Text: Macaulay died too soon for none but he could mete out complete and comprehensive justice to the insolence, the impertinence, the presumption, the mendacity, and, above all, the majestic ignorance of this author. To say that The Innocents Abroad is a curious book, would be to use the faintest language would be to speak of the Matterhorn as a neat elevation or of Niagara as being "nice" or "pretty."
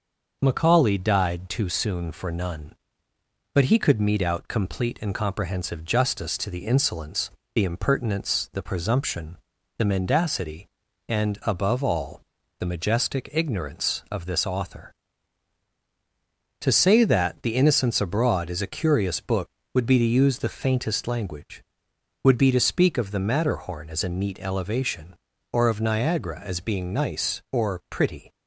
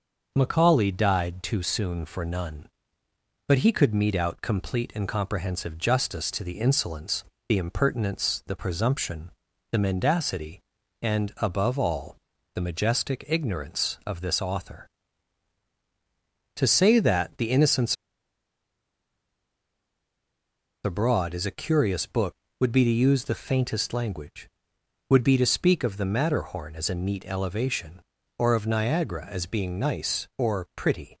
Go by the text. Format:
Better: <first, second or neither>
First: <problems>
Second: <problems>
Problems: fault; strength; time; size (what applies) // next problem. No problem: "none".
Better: first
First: starts louder than the rest; noticeable; until 1.4 s; 6 dB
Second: starts louder than the rest; noticeable; until 1.3 s; 6 dB // pauses between "Innocents" and "Abroad"; strong; at 17.9 s; 2.9 s long